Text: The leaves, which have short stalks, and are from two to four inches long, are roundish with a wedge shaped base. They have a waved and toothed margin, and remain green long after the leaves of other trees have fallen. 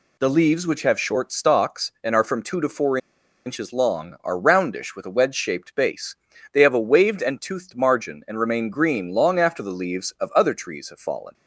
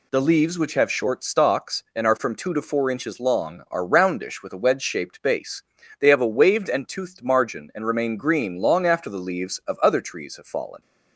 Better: second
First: pauses between "four" and "inches"; noticeable; at 2.9 s; 0.48 s long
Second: none

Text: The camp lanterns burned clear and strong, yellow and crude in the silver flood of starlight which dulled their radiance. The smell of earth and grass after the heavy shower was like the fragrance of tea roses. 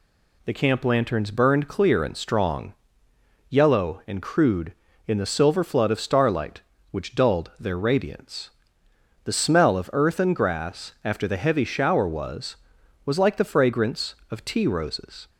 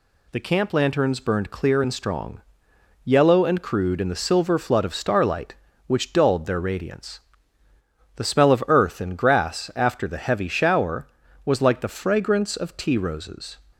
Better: second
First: says "was" twice; at 13.0 s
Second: none

